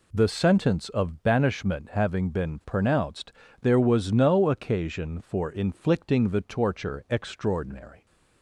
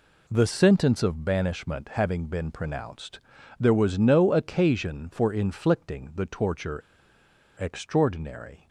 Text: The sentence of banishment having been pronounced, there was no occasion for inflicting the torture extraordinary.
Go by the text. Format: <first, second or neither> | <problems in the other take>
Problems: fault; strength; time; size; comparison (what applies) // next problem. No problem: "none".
first | pauses between "torture" and "extraordinary"; noticeable; at 6.8 s; 0.77 s long